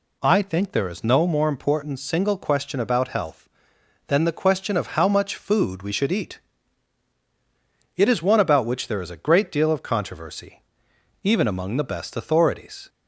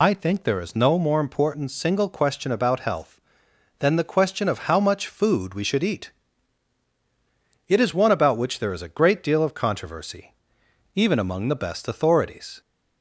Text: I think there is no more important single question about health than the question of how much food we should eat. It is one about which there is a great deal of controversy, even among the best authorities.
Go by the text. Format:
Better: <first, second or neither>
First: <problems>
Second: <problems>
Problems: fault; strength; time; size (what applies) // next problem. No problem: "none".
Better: first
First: none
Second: loses the start of "I"; at 0.0 s; 85 ms